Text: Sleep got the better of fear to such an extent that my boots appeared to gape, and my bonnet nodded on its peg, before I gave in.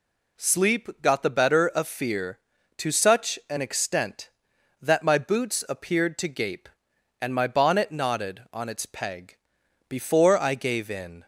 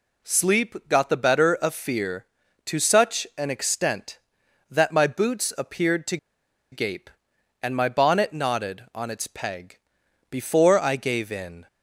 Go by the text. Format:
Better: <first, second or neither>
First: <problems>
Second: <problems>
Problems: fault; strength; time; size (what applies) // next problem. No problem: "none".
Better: first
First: none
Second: pauses between "to" and "gape"; noticeable; at 6.1 s; 0.55 s long